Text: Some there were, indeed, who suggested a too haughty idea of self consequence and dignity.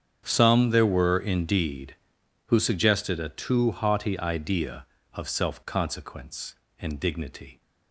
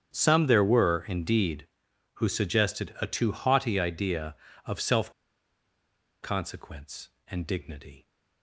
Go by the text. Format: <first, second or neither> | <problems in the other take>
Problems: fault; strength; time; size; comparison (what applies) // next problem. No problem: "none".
first | starts louder than the rest; strong; until 1.1 s; 8.5 dB; strong in the first // pauses between "self" and "consequence"; at 5.1 s; 1.1 s long